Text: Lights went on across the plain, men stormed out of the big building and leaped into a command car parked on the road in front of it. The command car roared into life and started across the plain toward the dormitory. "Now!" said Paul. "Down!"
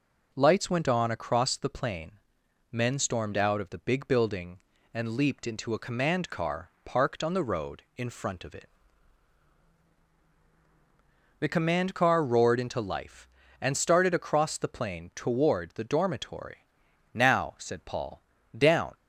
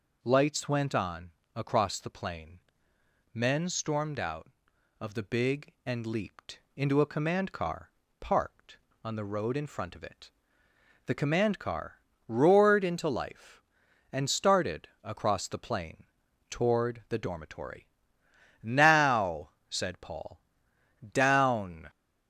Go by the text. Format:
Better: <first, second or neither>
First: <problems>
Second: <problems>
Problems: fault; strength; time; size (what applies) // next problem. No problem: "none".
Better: first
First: pauses between "car" and "parked"; slight; at 6.6 s; 0.16 s long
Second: pauses between "on" and "across"; slight; at 1.3 s; 0.24 s long // skips "building"; at 5.7 s // pauses between "leaped" and "into"; slight; at 6.6 s; 0.16 s long // pauses between "car" and "parked"; slight; at 7.9 s; 0.30 s long // pauses between "car" and "roared"; slight; at 12.0 s; 0.26 s long // pauses between "plain" and "toward"; noticeable; at 16.0 s; 0.46 s long